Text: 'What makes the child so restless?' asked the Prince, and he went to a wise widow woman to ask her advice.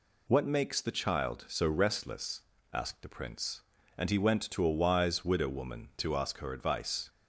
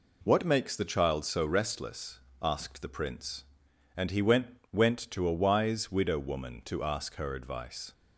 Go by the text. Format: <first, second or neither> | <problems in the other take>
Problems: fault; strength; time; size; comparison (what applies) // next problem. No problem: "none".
first | says "went" twice; at 4.7 s